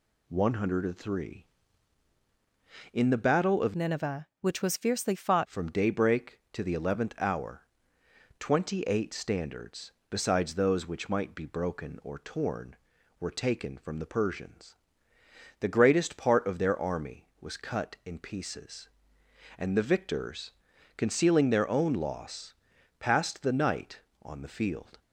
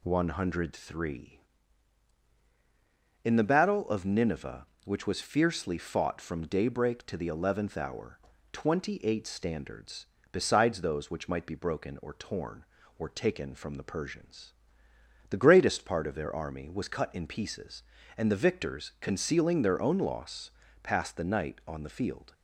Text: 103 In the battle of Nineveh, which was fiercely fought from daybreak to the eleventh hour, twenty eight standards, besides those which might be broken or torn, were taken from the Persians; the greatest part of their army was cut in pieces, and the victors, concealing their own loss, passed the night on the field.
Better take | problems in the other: second | changes voice from "Nineveh" to "fought"; from 3.7 to 5.4 s; 1.7 s long

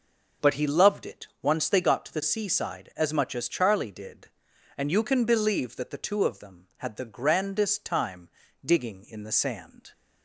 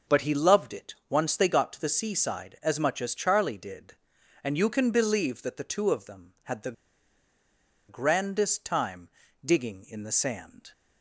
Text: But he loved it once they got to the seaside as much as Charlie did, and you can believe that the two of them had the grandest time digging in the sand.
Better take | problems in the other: first | pauses between "it" and "once"; slight; at 0.9 s; 0.16 s long; slight in the first // pauses between "the" and "grandest"; at 6.7 s; 1.1 s long // pauses between "time" and "digging"; slight; at 9.0 s; 0.36 s long; slight in the first

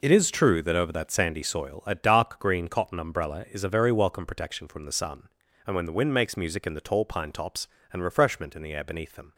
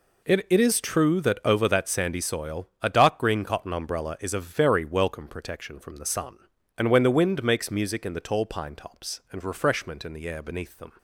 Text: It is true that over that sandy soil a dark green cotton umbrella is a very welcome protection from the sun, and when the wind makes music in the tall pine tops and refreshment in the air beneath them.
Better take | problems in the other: first | says "It" twice; at 0.4 s

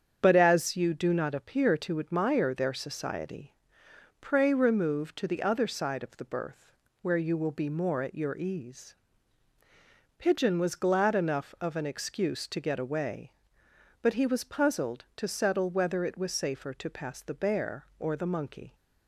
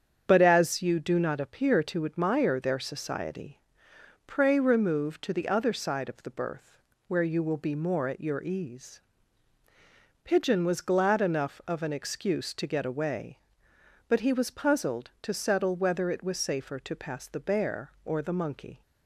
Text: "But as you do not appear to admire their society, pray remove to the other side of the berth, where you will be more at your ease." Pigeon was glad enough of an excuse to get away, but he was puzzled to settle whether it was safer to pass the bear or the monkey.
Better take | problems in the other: neither | starts louder than the rest; strong; the same in both

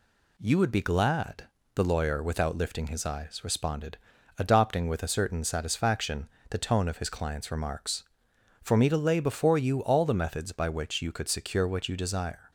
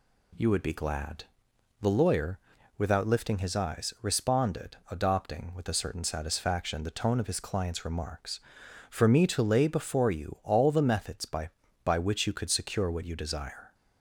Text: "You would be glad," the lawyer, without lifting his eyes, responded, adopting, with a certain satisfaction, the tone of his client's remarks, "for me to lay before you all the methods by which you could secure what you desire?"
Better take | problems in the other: first | says "by" twice; at 11.8 s

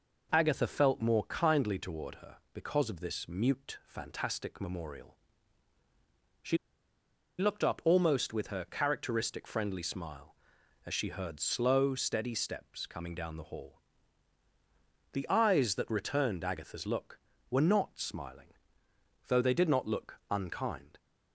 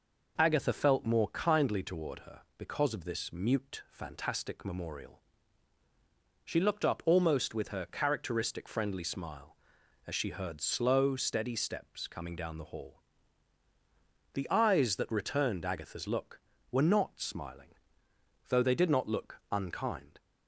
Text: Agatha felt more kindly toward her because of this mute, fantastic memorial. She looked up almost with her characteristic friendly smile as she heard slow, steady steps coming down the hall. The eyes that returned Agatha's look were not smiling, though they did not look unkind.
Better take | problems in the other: second | pauses between "She" and "looked"; noticeable; at 6.5 s; 0.82 s long

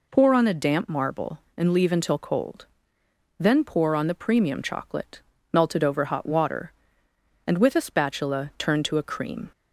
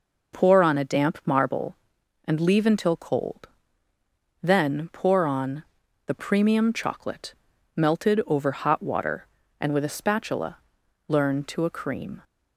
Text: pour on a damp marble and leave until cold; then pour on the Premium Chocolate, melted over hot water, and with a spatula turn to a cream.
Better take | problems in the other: first | pauses between "on" and "the"; at 5.6 s; 0.44 s long // says "learn" for "turn"; at 11.0 s

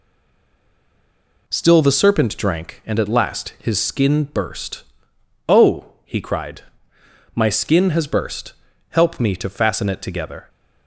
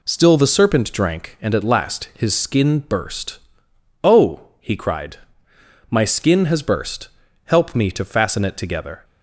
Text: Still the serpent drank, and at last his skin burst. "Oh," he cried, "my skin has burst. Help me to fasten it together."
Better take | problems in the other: second | stays silent before the first word; noticeable; until 1.4 s; 1.4 s long

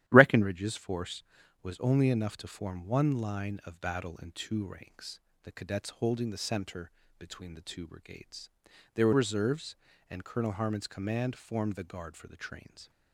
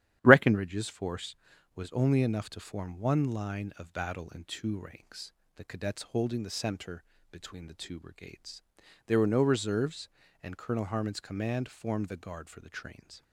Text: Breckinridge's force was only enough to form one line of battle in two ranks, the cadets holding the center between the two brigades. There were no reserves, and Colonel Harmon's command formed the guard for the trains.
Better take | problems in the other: second | starts louder than the rest; strong; until 1.0 s; 12.5 dB; strong in the second // pauses between "center" and "between"; slight; at 6.9 s; 0.28 s long; slight in the second // skips "no"; at 9.1 s

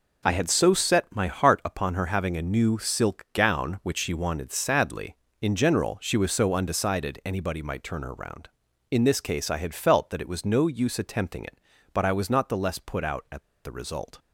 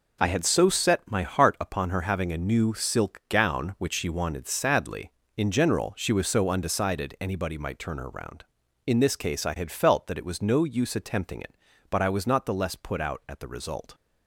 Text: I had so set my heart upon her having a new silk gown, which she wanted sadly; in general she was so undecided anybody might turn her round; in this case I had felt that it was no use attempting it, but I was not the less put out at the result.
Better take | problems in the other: second | pauses between "at" and "the"; slight; at 13.4 s; 0.22 s long

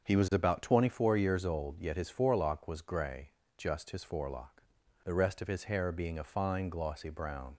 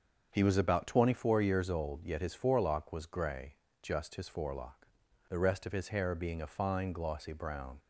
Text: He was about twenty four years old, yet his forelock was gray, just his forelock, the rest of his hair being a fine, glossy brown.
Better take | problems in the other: neither | starts louder than the rest; the same in both

